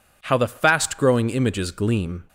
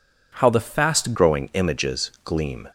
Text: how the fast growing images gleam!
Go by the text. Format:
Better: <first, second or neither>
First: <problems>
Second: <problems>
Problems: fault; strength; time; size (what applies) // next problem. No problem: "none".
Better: first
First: none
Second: changes voice at "growing"; from 1.1 s on; 1.5 s long